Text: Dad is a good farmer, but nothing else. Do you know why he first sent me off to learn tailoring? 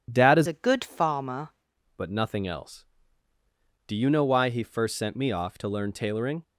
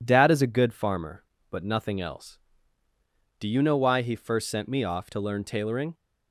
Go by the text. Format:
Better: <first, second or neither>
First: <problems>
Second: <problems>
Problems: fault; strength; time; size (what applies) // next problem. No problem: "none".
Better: second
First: changes voice from "a" to "farmer"; from 0.4 to 1.4 s; 1.0 s long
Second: none